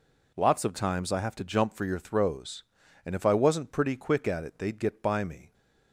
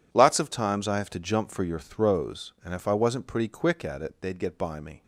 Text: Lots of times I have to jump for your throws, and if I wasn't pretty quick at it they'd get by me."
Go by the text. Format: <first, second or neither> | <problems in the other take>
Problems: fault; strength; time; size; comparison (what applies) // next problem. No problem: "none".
neither | none